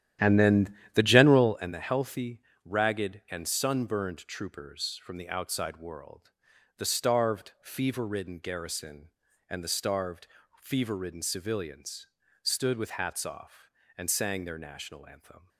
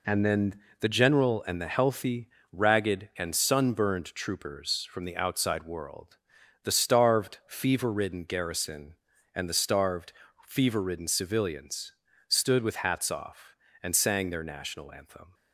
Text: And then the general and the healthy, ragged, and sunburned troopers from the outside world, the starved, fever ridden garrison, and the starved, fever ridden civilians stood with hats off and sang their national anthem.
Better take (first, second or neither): second